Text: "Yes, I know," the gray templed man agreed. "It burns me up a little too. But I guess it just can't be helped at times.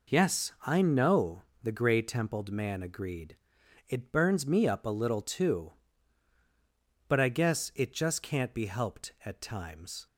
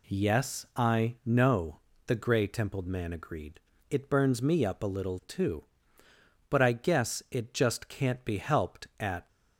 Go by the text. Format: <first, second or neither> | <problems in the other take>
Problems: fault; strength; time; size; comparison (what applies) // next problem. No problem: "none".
first | stops before "times"; at 9.2 s